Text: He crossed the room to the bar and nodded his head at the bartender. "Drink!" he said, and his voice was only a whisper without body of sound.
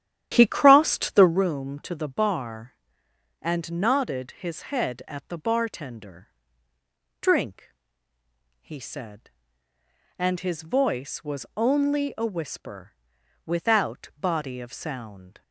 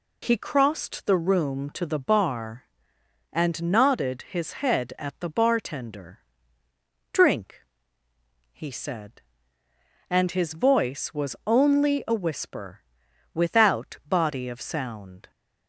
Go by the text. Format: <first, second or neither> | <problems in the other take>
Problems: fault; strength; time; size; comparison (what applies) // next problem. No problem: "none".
second | starts louder than the rest; strong; until 1.4 s; 11 dB // pauses between "whisper" and "without"; noticeable; at 12.9 s; 0.50 s long; noticeable in the second